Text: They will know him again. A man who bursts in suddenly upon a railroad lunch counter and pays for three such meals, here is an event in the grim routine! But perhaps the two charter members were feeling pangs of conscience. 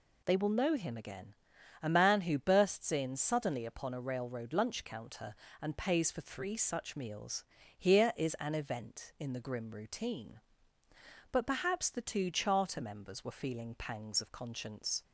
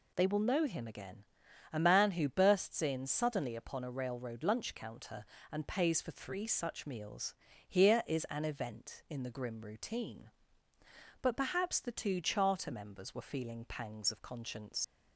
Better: first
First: none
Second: leaves "conscience" unfinished; at 14.8 s; 85 ms

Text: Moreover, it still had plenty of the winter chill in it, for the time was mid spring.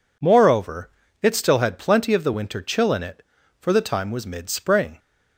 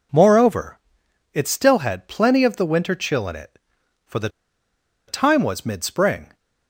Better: first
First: none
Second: pauses between "the" and "time"; noticeable; at 4.2 s; 0.78 s long

